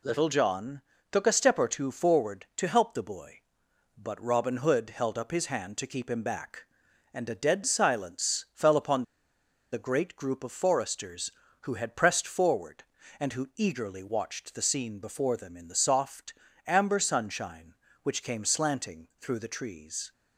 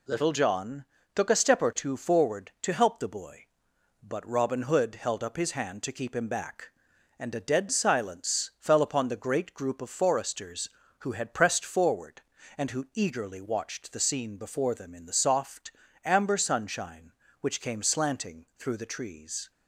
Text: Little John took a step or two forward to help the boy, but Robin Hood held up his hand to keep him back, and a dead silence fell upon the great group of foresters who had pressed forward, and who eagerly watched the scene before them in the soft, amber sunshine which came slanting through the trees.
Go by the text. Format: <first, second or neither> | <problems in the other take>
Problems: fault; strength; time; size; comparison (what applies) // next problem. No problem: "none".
second | pauses between "John" and "took"; slight; at 0.8 s; 0.32 s long; slight in the second // pauses between "upon" and "the"; noticeable; at 9.0 s; 0.69 s long